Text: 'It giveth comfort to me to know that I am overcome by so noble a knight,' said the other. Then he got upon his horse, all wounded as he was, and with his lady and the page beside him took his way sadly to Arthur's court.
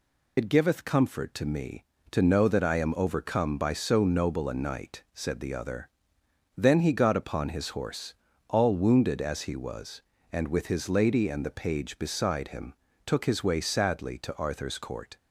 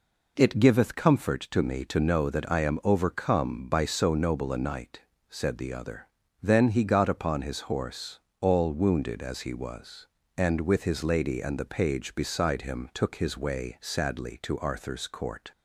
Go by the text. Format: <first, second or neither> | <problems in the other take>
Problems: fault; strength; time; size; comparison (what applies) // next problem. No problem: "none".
second | loses the start of "It"; at 0.3 s; 70 ms // pauses between "him" and "took"; slight; at 12.7 s; 0.32 s long